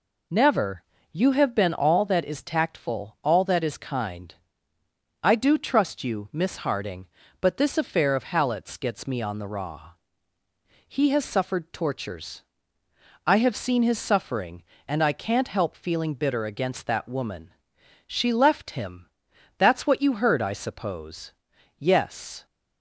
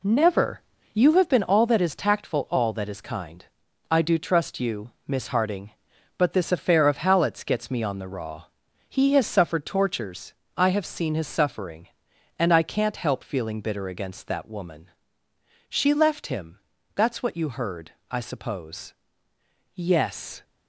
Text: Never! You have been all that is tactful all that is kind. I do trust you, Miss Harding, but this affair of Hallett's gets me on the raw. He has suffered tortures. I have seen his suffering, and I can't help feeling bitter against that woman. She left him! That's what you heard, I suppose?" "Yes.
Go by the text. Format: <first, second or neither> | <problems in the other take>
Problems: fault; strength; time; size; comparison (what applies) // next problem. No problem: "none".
first | gets quieter; throughout; 6.5 dB